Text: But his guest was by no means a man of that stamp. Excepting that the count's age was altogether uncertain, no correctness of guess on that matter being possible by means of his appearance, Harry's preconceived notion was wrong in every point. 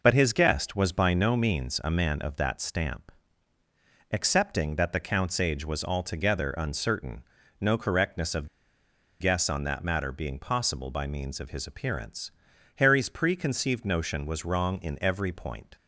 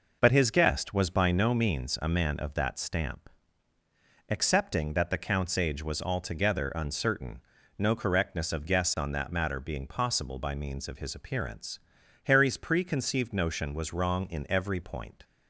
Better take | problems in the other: second | pauses between "of" and "guess"; noticeable; at 8.4 s; 0.72 s long

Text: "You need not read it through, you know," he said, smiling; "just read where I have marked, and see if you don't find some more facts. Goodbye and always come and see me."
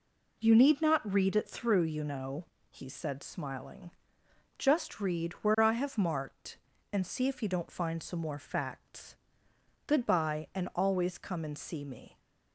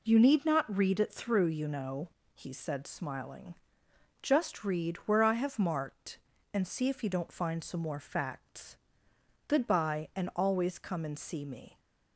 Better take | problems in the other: neither | none

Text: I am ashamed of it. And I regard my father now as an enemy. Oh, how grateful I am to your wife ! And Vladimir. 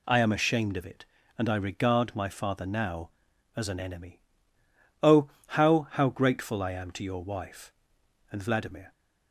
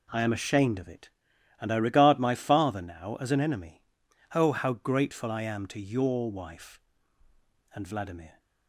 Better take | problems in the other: second | says "how" twice; at 5.9 s

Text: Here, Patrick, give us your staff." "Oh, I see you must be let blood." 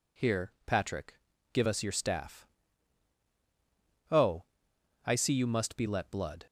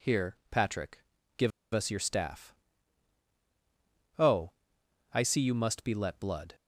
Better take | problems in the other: first | pauses between "give" and "us"; slight; at 1.5 s; 0.24 s long

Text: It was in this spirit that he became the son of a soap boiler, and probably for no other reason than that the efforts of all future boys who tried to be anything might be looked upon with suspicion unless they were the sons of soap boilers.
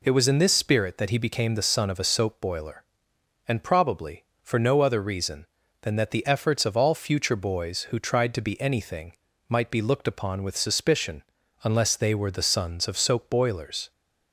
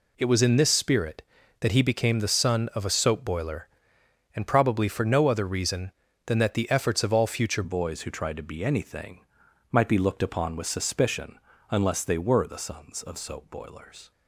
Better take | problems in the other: first | changes voice at "boys"; from 7.6 s on; 6.5 s long // pauses between "anything" and "might"; noticeable; at 9.2 s; 0.50 s long; slight in the first // pauses between "suspicion" and "unless"; slight; at 11.3 s; 0.32 s long; also in the first

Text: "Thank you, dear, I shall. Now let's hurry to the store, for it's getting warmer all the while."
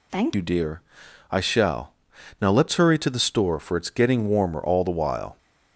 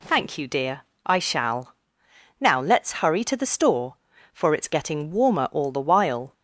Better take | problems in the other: second | changes voice at "you"; from 0.3 s on; 5.0 s long

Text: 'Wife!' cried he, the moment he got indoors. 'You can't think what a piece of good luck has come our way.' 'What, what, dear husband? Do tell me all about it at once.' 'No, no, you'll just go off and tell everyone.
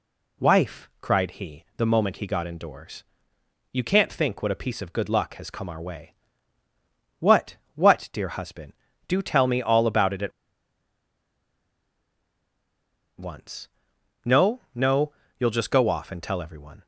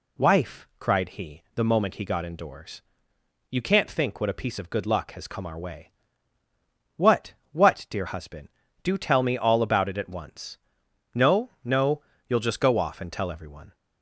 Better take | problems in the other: second | pauses between "at" and "once"; strong; at 10.3 s; 2.8 s long

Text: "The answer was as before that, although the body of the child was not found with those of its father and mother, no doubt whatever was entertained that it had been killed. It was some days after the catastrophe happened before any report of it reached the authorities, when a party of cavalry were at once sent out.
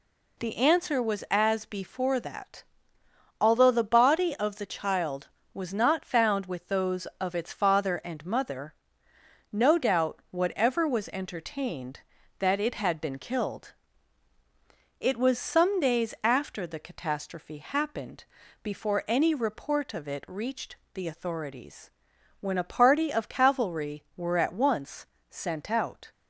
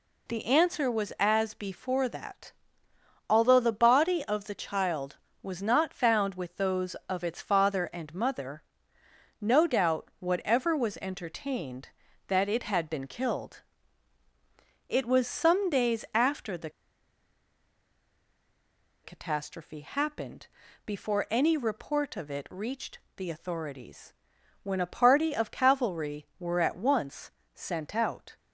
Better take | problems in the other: first | pauses between "the" and "catastrophe"; strong; at 16.6 s; 2.3 s long // pauses between "happened" and "before"; at 20.4 s; 0.38 s long; also in the first // pauses between "reached" and "the"; slight; at 22.9 s; 0.18 s long; slight in the first // pauses between "once" and "sent"; slight; at 27.3 s; 0.22 s long; slight in the first

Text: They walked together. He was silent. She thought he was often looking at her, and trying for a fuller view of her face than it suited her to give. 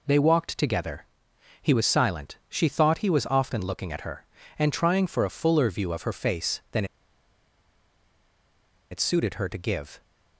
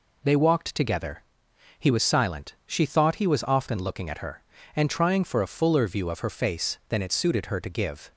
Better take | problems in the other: second | pauses between "than" and "it"; strong; at 6.8 s; 2.0 s long

